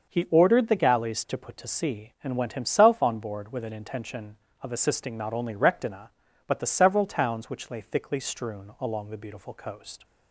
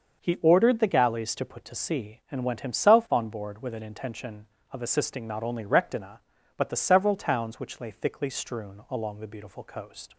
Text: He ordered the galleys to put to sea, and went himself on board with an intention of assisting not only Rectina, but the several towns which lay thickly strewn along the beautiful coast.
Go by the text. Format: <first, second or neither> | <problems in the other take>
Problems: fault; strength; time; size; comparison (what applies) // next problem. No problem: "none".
neither | starts louder than the rest; the same in both